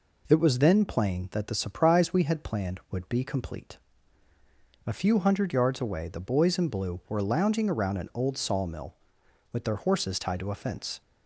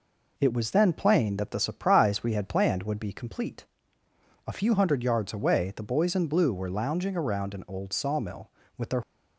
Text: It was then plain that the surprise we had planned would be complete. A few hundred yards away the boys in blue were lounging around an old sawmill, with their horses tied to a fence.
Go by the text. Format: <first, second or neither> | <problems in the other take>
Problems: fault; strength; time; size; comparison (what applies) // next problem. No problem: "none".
first | stops before "horses tied to a fence"; at 9.0 s